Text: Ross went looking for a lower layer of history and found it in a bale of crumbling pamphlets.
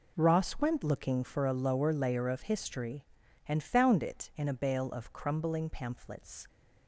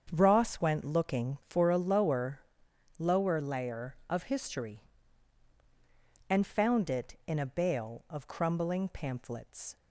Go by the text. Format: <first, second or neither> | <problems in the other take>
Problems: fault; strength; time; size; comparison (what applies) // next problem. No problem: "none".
first | starts louder than the rest; strong; until 1.1 s; 7.5 dB // says "lower" twice; at 2.9 s